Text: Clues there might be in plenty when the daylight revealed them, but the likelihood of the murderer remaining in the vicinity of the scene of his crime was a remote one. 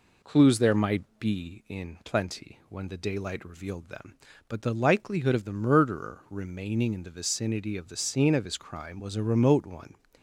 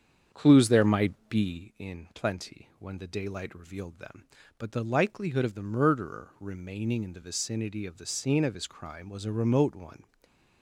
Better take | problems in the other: first | starts louder than the rest; strong; until 1.6 s; 8 dB // pauses between "might" and "be"; slight; at 1.1 s; 0.16 s long; slight in the first // stays silent after the last word; slight; from 10.0 s on; 0.6 s long

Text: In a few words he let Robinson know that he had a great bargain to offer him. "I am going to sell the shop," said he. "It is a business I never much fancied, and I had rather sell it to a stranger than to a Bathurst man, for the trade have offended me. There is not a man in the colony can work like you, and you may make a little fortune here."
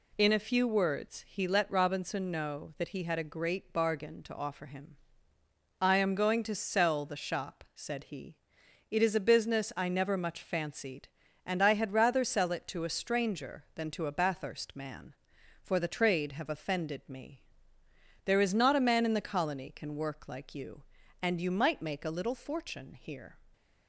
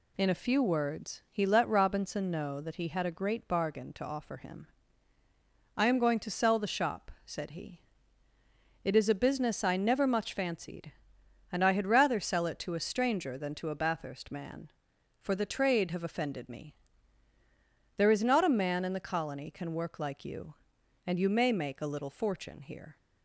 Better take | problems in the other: second | says "might" for "may"; at 21.5 s

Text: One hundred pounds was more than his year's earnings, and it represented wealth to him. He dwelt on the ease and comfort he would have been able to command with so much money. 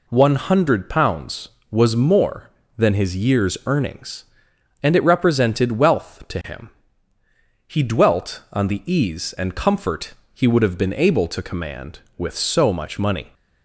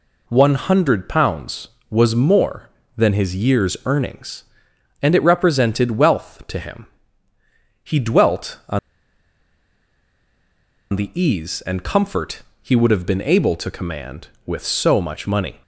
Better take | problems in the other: first | pauses between "on" and "the"; strong; at 8.7 s; 2.1 s long // pauses between "comfort" and "he"; slight; at 12.4 s; 0.20 s long; slight in the first

